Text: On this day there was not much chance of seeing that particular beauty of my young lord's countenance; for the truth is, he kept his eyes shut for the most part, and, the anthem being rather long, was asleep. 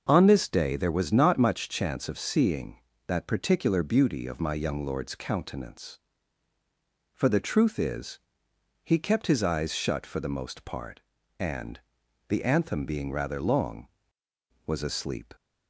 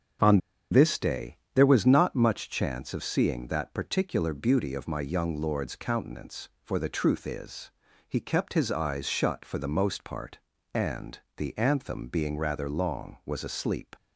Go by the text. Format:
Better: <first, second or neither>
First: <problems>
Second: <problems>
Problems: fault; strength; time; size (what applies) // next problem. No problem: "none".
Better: first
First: starts louder than the rest; until 1.0 s; 6 dB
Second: starts louder than the rest; strong; until 1.7 s; 7.5 dB // pauses between "On" and "this"; slight; at 0.4 s; 0.32 s long // pauses between "day" and "there"; slight; at 1.3 s; 0.16 s long